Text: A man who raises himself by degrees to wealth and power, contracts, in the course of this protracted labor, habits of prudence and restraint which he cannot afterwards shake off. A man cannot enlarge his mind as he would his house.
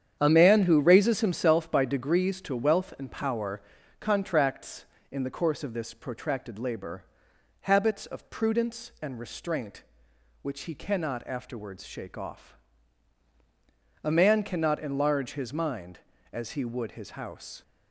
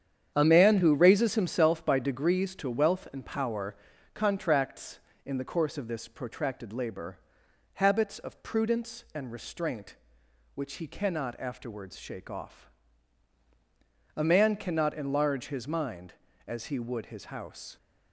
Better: neither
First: starts louder than the rest; strong; until 1.2 s; 8.5 dB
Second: starts louder than the rest; strong; until 1.3 s; 8.5 dB

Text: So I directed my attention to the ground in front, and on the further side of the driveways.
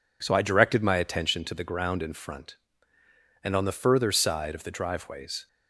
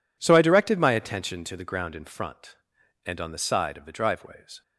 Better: first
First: none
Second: skips "further"; at 3.3 s

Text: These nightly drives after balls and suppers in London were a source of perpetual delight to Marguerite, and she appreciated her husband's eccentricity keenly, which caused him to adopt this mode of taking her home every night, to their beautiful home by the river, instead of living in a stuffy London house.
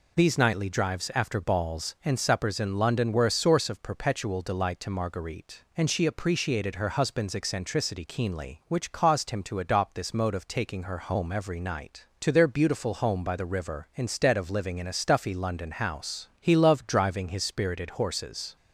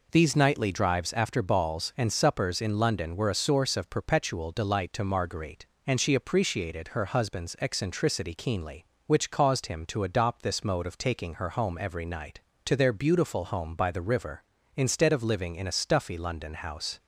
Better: second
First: goes on to say "He loved driving his spirited horses"; strong; from 16.3 s on; 2.1 s long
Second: none

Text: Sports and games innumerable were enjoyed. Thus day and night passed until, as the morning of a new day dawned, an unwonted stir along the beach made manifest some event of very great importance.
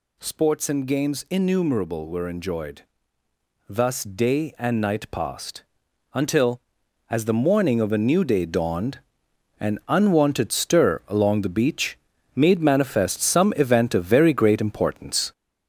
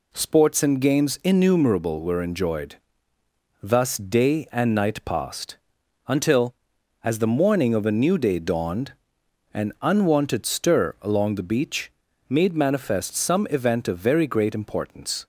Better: second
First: gets louder; noticeable; throughout; 5 dB // pauses between "passed" and "until"; noticeable; at 5.6 s; 0.48 s long // pauses between "beach" and "made"; at 11.9 s; 0.38 s long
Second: pauses between "passed" and "until"; noticeable; at 5.5 s; 0.48 s long // pauses between "beach" and "made"; at 11.8 s; 0.38 s long

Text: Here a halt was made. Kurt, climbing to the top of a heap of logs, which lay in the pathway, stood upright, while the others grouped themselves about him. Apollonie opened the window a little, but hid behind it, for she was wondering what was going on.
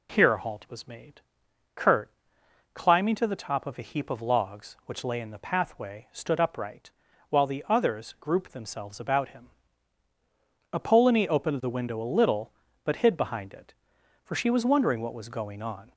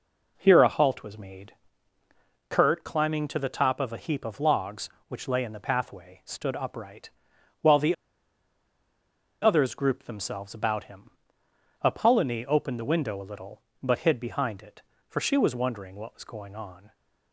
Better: first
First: none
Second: pauses between "the" and "others"; strong; at 7.9 s; 1.4 s long

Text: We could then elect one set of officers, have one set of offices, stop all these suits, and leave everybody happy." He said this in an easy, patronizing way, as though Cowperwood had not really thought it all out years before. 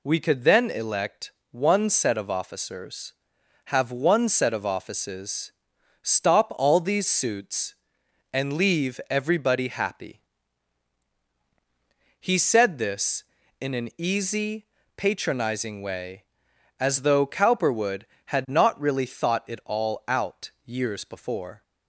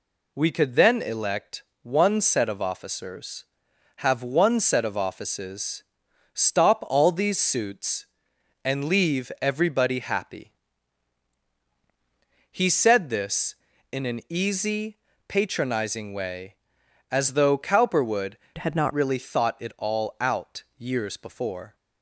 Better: first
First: pauses between "elect" and "one"; slight; at 1.3 s; 0.20 s long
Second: pauses between "elect" and "one"; slight; at 1.6 s; 0.20 s long // changes voice from "had" to "not"; from 18.5 to 18.9 s; 0.4 s long

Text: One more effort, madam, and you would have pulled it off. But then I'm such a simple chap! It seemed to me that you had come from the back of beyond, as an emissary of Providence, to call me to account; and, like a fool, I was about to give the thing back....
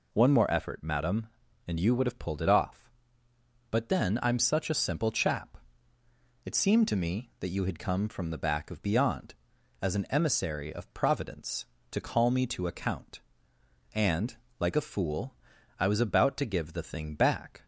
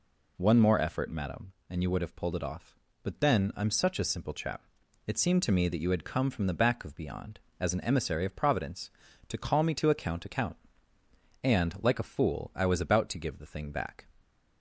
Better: first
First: none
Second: says "account" twice; at 10.2 s

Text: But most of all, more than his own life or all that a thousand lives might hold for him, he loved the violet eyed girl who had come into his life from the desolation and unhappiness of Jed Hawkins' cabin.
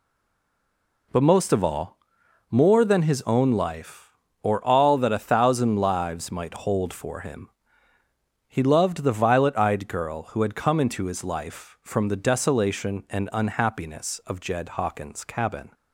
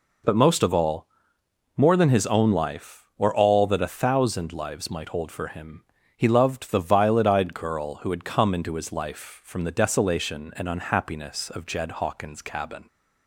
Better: second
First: stays silent before the first word; until 1.1 s; 1.1 s long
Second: none

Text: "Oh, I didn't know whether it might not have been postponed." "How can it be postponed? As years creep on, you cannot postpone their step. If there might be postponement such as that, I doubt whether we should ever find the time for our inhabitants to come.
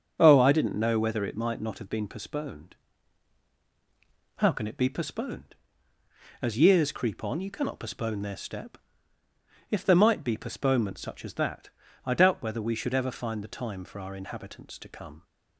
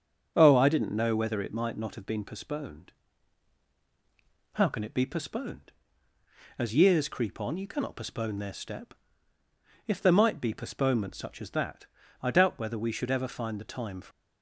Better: first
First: starts louder than the rest; until 1.2 s; 7 dB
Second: starts louder than the rest; until 1.3 s; 7 dB // stops before "our inhabitants to come"; at 14.1 s

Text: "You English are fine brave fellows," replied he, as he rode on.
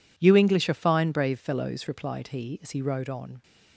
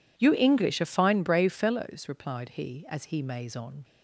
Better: first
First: none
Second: says "maze" for "rode"; at 3.2 s

